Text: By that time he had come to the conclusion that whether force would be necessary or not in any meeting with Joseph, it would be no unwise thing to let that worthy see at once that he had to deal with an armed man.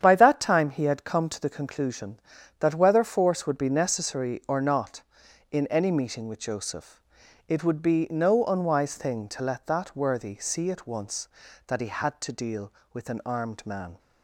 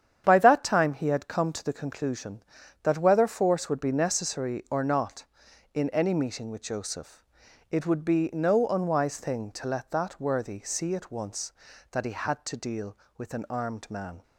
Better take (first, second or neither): neither